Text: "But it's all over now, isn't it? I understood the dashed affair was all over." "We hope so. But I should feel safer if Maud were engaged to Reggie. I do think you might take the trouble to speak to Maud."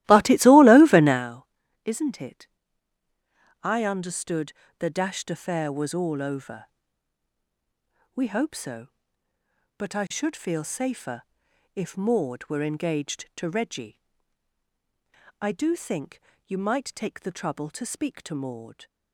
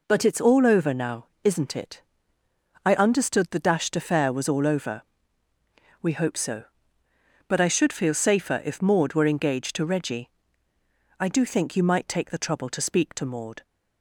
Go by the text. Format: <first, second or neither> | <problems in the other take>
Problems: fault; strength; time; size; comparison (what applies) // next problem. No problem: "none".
second | starts louder than the rest; strong; until 1.3 s; 15.5 dB // pauses between "understood" and "the"; slight; at 4.5 s; 0.28 s long // pauses between "safer" and "if"; noticeable; at 11.2 s; 0.50 s long // pauses between "think" and "you"; slight; at 16.1 s; 0.26 s long